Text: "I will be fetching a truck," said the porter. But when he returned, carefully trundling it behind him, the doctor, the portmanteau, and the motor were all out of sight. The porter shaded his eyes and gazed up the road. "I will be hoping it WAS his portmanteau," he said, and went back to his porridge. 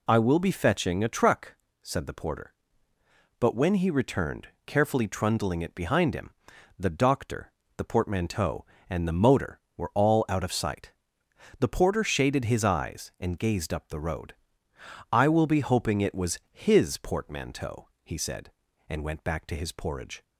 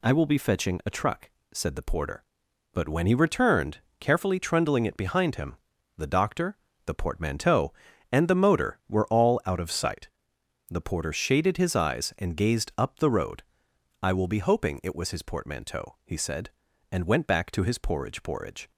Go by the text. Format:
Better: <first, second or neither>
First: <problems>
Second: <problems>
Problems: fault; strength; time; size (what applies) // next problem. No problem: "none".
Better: first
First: none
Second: says "porridge" twice; at 18.2 s